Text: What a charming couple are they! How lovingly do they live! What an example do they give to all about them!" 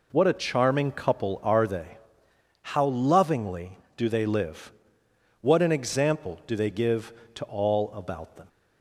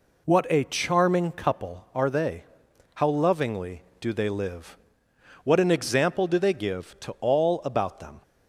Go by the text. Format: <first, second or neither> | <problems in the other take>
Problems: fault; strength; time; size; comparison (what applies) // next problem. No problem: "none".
neither | none